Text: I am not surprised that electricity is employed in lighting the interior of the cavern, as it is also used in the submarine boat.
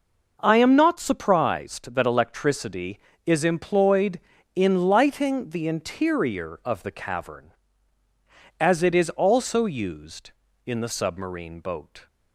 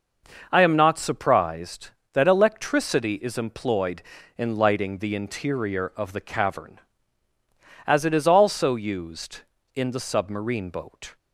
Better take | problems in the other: neither | none

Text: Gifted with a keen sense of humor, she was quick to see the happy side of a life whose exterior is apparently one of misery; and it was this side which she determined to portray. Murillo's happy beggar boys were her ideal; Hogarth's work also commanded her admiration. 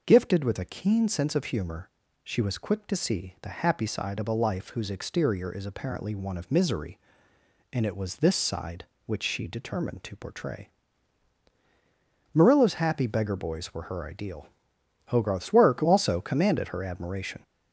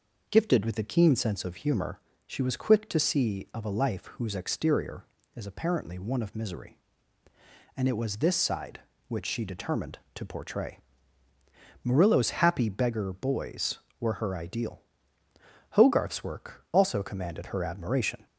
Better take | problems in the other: first | skips "the happy side"; at 3.5 s

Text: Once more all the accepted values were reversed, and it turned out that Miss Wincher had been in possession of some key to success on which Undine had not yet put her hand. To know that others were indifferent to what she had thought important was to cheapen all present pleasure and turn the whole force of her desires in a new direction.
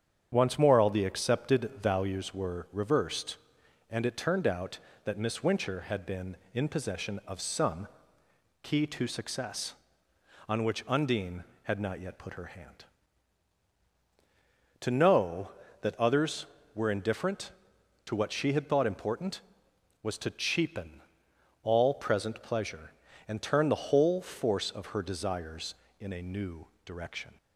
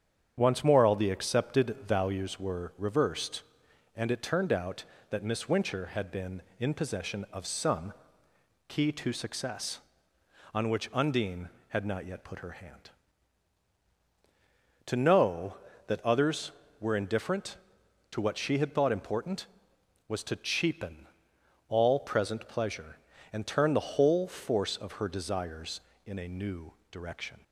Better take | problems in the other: neither | starts louder than the rest; strong; the same in both // pauses between "some" and "key"; noticeable; the same in both // pauses between "cheapen" and "all"; noticeable; the same in both // pauses between "new" and "direction"; slight; the same in both

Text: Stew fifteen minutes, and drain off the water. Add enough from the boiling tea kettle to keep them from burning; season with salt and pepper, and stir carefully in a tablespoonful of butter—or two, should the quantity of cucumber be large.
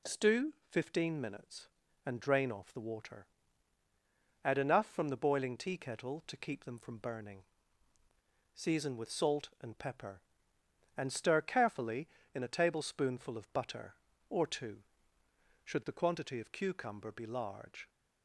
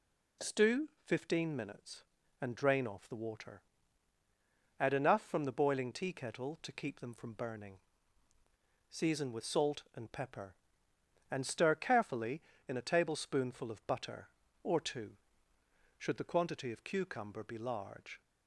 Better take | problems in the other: neither | pauses between "Stew" and "fifteen"; slight; the same in both

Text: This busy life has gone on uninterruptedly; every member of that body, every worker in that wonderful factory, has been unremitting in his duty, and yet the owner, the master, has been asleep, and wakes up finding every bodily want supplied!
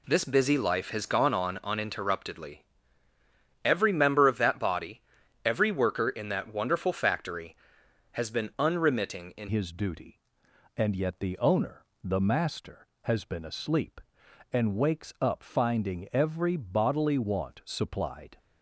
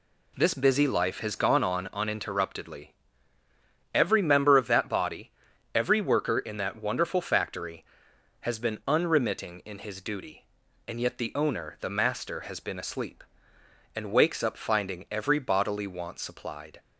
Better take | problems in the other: second | changes voice at "his"; from 9.4 s on; 8.9 s long

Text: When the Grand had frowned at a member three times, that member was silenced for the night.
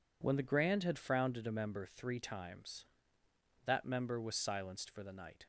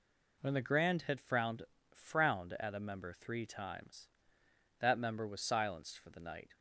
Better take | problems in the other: first | says "frowned" twice; at 1.9 s

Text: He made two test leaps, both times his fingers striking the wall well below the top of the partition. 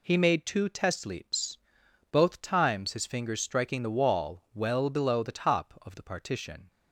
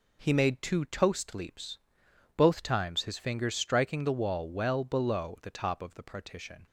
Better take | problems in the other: first | says "toast" for "test"; at 0.8 s

